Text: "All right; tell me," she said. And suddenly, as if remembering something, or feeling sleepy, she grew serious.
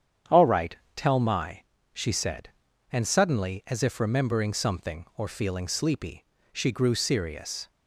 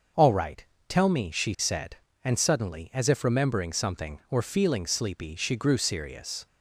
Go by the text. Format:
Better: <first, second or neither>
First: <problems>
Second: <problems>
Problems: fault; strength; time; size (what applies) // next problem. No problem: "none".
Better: second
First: starts louder than the rest; strong; until 1.5 s; 8.5 dB // says "my" for "me"; at 1.2 s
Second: starts louder than the rest; until 1.3 s; 6 dB